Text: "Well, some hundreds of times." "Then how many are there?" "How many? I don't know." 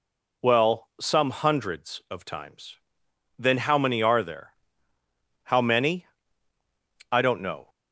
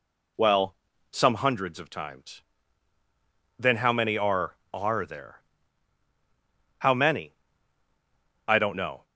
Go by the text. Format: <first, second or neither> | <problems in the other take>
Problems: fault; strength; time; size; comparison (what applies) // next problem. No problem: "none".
first | says "are" twice; at 4.7 s